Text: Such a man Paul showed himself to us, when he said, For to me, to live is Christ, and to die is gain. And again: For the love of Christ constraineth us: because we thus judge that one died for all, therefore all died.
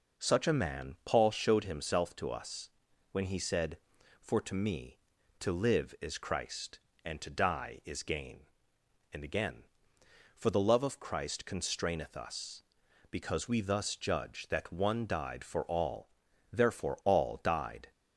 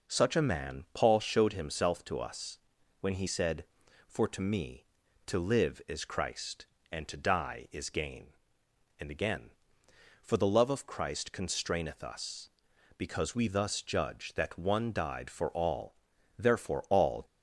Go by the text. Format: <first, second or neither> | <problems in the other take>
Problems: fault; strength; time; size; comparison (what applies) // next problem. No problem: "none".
first | stops before "died"; at 17.2 s